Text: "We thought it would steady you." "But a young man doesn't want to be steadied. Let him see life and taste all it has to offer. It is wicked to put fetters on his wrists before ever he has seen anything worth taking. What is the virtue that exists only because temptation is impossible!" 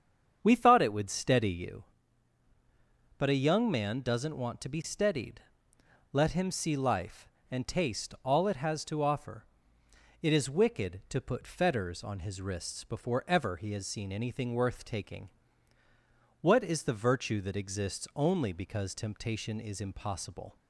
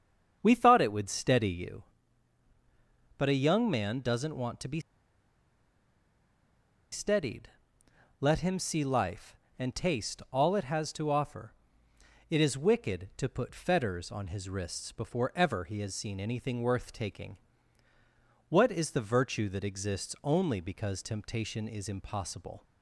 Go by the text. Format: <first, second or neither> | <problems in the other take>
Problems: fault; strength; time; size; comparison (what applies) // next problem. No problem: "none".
first | starts louder than the rest; strong; until 1.4 s; 7.5 dB; strong in the first // pauses between "be" and "steadied"; strong; at 4.7 s; 2.1 s long